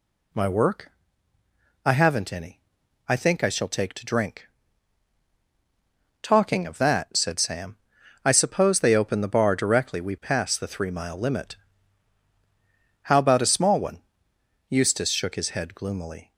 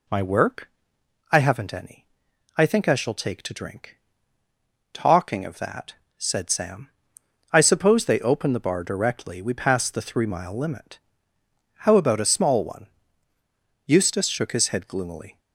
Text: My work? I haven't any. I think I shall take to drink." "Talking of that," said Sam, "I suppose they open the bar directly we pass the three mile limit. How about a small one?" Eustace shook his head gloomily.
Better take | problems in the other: neither | none

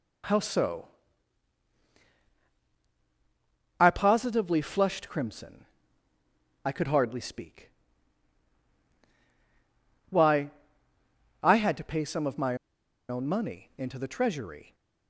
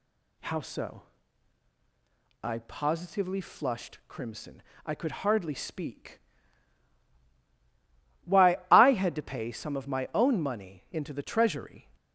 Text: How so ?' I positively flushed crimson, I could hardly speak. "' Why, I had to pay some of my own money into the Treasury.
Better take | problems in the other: second | pauses between "my" and "own"; noticeable; at 12.5 s; 0.52 s long

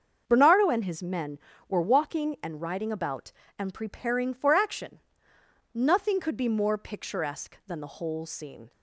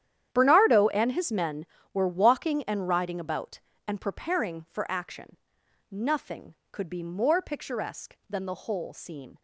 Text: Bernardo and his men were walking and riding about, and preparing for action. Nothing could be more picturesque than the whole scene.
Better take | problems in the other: first | gets quieter; strong; throughout; 16 dB // starts louder than the rest; strong; until 1.3 s; 10 dB; also in the first

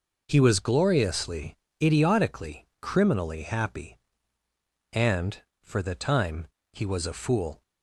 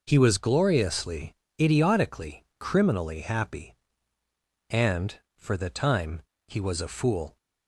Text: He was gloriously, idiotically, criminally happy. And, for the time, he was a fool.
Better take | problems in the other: neither | none

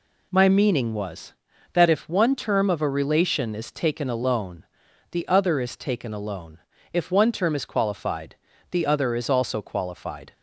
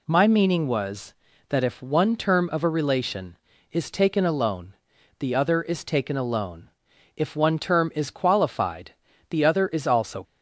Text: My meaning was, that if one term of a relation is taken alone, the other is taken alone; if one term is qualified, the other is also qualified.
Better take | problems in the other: first | stops before "qualified"; at 10.2 s

